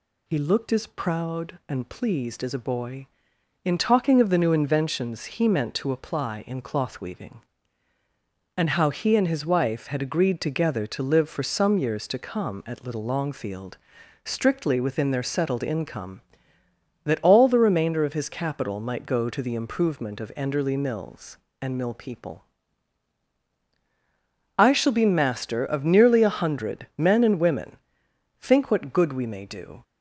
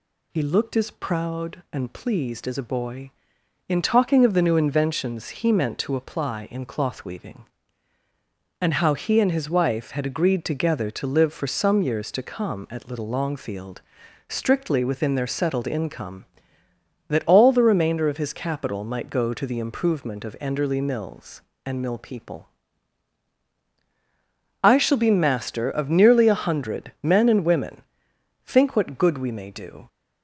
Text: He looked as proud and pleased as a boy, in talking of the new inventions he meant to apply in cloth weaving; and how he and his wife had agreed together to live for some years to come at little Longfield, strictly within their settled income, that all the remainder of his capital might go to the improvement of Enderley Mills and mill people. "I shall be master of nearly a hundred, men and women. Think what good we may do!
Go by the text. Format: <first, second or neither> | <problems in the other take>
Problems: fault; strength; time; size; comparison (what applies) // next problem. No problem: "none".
neither | none